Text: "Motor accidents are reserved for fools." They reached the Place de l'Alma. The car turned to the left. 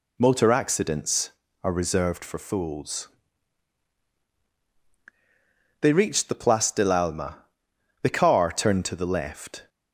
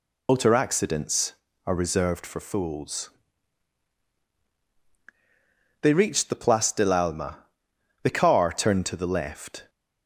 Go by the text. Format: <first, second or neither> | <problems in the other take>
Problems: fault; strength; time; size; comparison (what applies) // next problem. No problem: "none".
first | loses the start of "Motor"; at 0.2 s; 70 ms